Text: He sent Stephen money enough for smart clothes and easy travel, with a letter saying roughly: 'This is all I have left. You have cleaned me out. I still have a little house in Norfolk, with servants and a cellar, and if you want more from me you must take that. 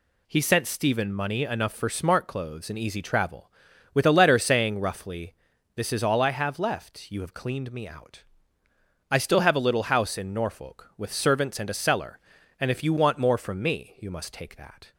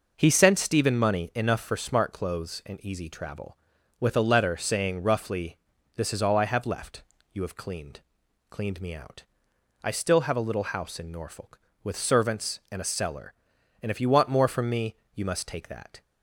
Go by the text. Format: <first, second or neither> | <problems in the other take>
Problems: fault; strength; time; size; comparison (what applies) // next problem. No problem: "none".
first | says "cleaned" twice; at 8.5 s // pauses between "me" and "you"; slight; at 14.9 s; 0.22 s long